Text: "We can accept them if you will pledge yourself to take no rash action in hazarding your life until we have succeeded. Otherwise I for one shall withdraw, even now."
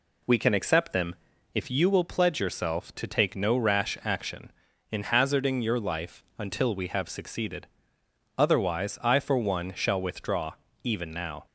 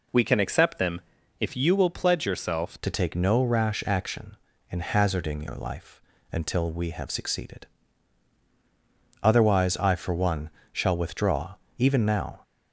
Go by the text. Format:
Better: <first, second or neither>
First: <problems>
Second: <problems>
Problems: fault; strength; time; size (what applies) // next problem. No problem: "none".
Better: first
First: pauses between "them" and "if"; at 1.1 s; 0.38 s long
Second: pauses between "them" and "if"; at 1.0 s; 0.38 s long // changes voice at "to"; from 2.8 s on; 9.6 s long // pauses between "life" and "until"; slight; at 6.0 s; 0.30 s long // pauses between "one" and "shall"; slight; at 10.4 s; 0.24 s long